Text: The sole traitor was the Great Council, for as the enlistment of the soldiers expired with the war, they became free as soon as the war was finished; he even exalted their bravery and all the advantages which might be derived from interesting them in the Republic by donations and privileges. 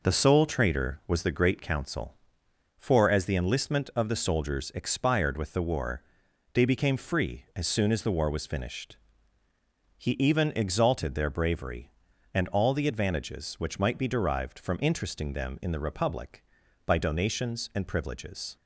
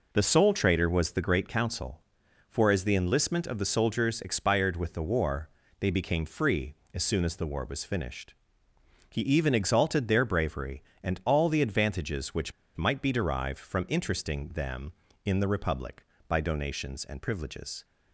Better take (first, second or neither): first